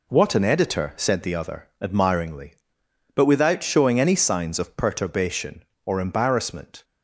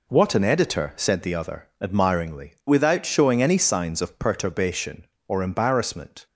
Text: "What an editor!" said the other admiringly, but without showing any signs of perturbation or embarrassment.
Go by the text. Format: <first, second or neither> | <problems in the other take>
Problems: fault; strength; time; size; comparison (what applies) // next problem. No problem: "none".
first | skips "but"; at 2.6 s